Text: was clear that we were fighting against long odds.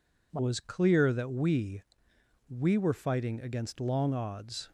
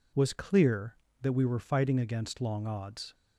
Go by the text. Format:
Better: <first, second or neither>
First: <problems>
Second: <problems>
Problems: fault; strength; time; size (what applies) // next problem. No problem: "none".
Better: second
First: says "we" twice; at 2.4 s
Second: none